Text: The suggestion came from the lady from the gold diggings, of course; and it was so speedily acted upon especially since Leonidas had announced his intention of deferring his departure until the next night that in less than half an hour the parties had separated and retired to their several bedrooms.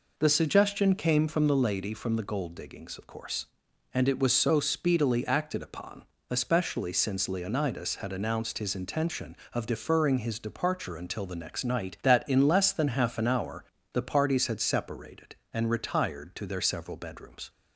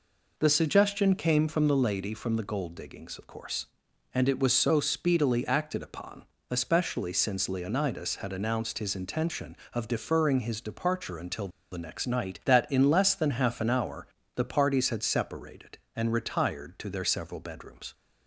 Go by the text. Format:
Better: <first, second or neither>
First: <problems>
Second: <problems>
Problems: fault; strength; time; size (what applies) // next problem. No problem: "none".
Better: first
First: pauses between "upon" and "especially"; slight; at 6.0 s; 0.24 s long // pauses between "hour" and "the"; slight; at 13.6 s; 0.30 s long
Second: pauses between "upon" and "especially"; slight; at 6.2 s; 0.24 s long // pauses between "until" and "the"; slight; at 11.4 s; 0.23 s long // pauses between "hour" and "the"; slight; at 14.0 s; 0.30 s long